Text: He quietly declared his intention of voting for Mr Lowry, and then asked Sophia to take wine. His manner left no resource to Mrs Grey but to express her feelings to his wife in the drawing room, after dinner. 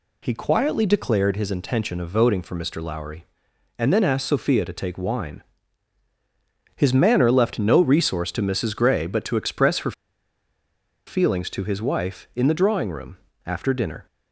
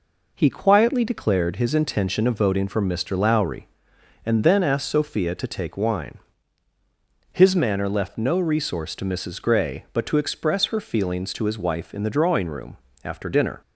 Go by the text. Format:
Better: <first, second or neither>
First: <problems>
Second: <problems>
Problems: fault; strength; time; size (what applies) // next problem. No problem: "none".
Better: second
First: pauses between "her" and "feelings"; at 9.9 s; 1.1 s long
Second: none